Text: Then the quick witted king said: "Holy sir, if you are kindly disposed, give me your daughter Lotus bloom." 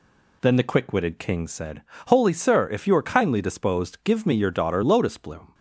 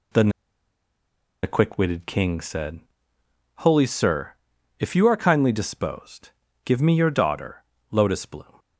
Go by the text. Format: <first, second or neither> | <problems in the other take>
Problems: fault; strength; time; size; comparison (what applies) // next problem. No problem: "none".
first | pauses between "Then" and "the"; at 0.2 s; 1.1 s long // pauses between "daughter" and "Lotus"; slight; at 7.6 s; 0.28 s long